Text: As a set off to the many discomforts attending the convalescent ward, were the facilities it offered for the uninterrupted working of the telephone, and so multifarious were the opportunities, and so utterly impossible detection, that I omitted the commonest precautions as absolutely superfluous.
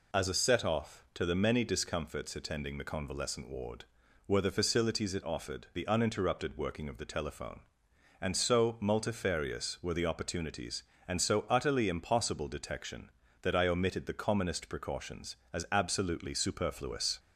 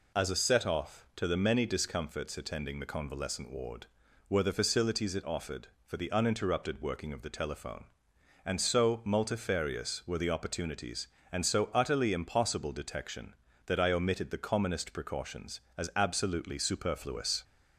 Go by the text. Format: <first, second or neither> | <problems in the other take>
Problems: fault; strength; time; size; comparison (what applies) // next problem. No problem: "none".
second | skips "for"; at 5.7 s